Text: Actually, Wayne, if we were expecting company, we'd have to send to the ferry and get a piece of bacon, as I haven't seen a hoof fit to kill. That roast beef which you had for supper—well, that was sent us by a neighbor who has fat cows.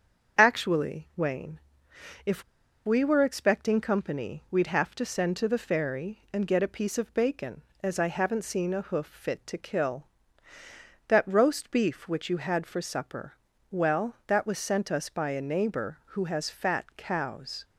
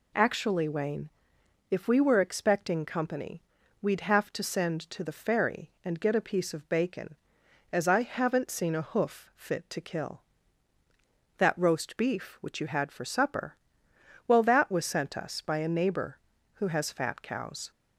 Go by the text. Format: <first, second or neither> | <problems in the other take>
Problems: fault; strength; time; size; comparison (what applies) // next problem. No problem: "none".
second | starts louder than the rest; until 1.4 s; 7 dB // pauses between "if" and "we"; at 2.4 s; 0.43 s long